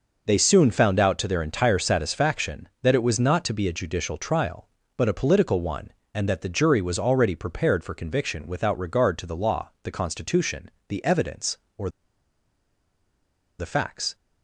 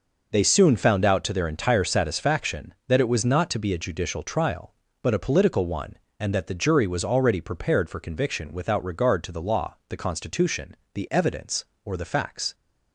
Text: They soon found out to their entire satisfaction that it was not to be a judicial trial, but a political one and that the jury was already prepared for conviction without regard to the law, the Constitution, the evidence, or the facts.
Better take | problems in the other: second | pauses between "or" and "the"; strong; at 11.8 s; 1.7 s long

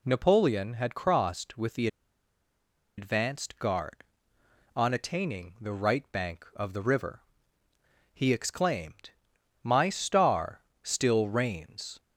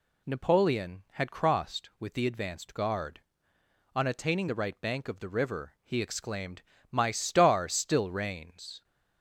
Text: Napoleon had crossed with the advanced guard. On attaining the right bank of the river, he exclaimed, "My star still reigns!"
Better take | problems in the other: second | pauses between "the" and "advanced"; at 1.8 s; 1.1 s long // pauses between "star" and "still"; slight; at 10.6 s; 0.22 s long

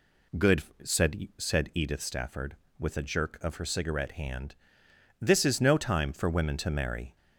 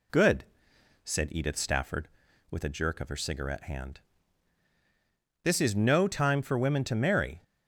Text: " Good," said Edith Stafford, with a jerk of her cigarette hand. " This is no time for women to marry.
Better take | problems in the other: second | says "said" twice; at 1.3 s

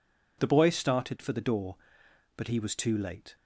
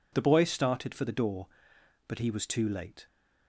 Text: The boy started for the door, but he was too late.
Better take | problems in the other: neither | none

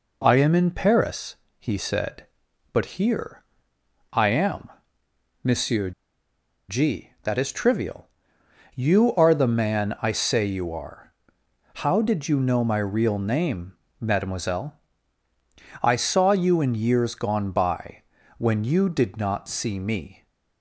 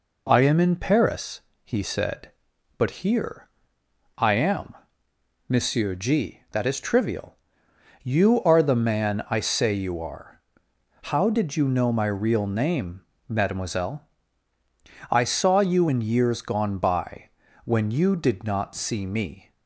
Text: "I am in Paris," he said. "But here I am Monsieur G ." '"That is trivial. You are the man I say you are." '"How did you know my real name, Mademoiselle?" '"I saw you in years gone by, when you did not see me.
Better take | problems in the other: second | pauses between "here" and "I"; noticeable; at 3.4 s; 0.70 s long; noticeable in the second // pauses between "am" and "Monsieur"; noticeable; at 4.7 s; 0.72 s long; noticeable in the second // pauses between "Monsieur" and "G"; noticeable; at 5.9 s; 0.78 s long

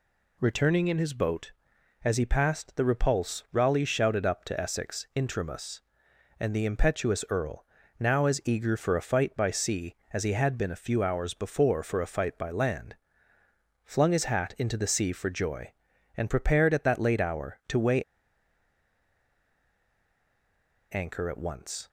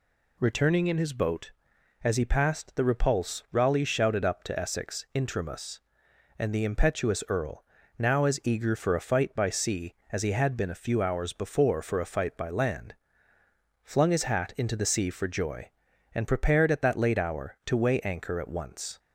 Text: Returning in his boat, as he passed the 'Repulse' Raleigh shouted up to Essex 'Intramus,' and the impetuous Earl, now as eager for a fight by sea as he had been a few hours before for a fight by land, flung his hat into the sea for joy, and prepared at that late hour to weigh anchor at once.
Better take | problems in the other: second | pauses between "weigh" and "anchor"; strong; at 18.0 s; 2.8 s long

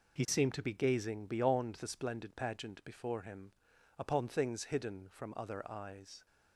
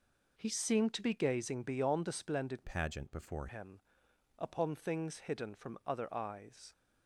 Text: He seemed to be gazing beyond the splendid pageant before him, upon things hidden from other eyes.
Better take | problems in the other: first | changes voice from "pageant" to "before"; from 2.6 to 3.4 s; 0.8 s long

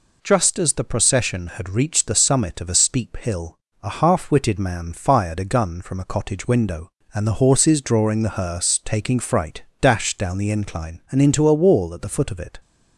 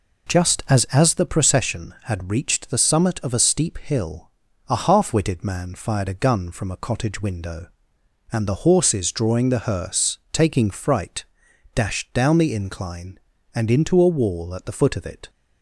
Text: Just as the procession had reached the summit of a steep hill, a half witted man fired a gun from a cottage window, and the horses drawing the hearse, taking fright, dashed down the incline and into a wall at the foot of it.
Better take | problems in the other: first | says "as" twice; at 0.8 s

